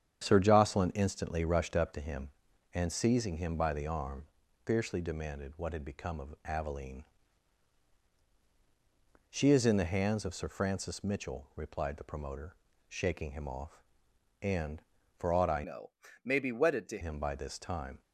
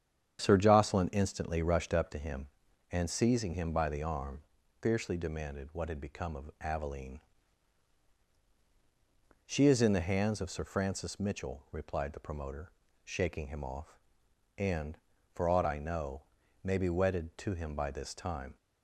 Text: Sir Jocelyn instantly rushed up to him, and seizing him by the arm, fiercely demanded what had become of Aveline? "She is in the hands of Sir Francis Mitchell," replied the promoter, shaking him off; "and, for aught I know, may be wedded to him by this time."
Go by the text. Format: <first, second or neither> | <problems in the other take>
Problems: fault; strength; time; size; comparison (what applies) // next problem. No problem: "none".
second | starts louder than the rest; strong; until 1.2 s; 8.5 dB; strong in the second // changes voice from "know" to "to"; from 15.6 to 16.9 s; 1.3 s long